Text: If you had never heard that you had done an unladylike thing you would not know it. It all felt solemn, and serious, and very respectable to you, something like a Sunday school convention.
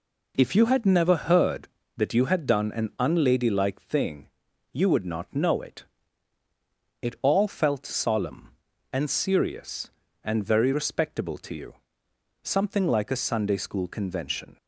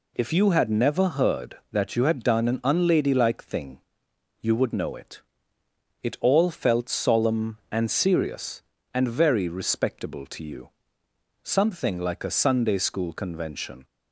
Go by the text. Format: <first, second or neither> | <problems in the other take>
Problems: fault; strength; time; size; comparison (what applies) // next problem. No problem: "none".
first | pauses between "thing" and "you"; noticeable; at 3.7 s; 0.62 s long; noticeable in the first // skips "not"; at 4.7 s